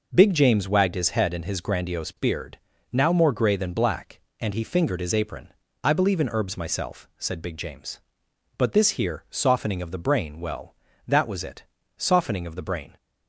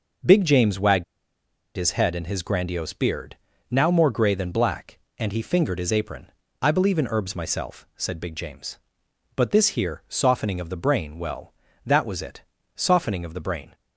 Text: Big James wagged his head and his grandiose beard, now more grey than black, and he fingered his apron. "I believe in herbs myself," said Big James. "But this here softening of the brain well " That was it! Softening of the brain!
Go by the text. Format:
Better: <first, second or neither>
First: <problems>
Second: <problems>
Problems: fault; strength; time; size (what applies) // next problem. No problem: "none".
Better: first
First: none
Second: pauses between "wagged" and "his"; noticeable; at 1.0 s; 0.72 s long